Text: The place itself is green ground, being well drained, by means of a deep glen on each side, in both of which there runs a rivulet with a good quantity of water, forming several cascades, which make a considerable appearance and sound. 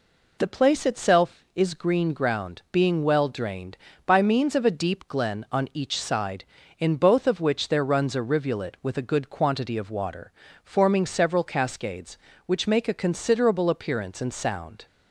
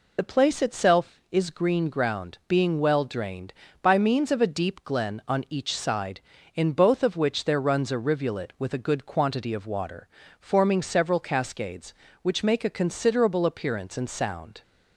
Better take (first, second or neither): first